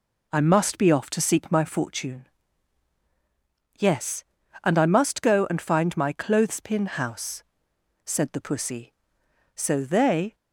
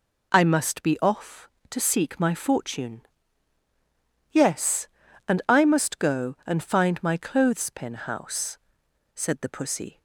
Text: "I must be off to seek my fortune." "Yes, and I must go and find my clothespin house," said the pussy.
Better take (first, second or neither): second